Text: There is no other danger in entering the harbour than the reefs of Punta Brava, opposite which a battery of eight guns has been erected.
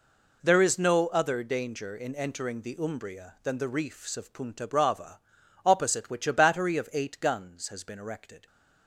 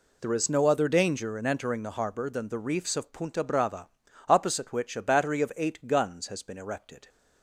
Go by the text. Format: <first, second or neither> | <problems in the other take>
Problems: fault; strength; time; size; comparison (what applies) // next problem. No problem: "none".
second | says "umbria" for "harbour"; at 2.7 s